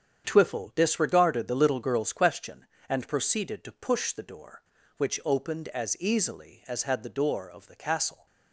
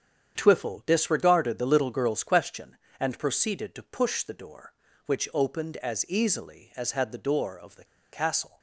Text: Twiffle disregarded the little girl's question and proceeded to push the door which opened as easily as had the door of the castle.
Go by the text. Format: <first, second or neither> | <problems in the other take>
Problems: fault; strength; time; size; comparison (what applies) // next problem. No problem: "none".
first | starts louder than the rest; strong; until 1.3 s; 8 dB; strong in the first // pauses between "the" and "castle"; slight; at 7.8 s; 0.27 s long